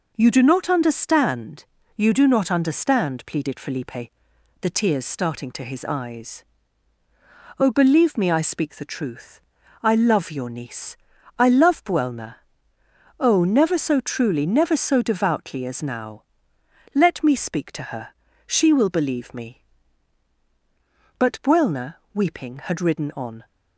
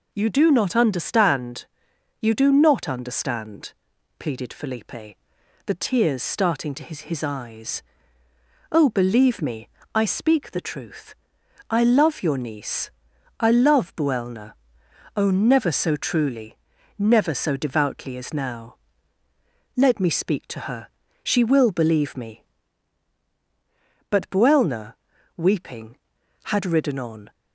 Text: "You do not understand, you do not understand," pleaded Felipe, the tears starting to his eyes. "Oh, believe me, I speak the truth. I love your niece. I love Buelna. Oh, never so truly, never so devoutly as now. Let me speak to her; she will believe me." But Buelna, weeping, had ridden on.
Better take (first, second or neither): first